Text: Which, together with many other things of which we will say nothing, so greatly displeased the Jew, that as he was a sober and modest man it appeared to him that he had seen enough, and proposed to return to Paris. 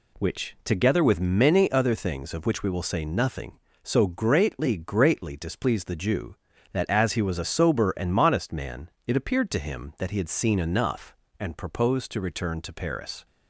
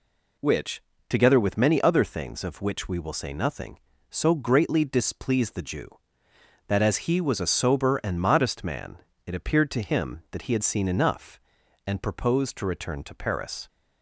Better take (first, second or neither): second